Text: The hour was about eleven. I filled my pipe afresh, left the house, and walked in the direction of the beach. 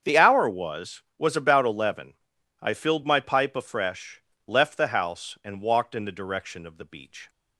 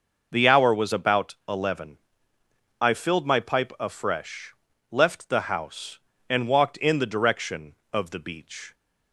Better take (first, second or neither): second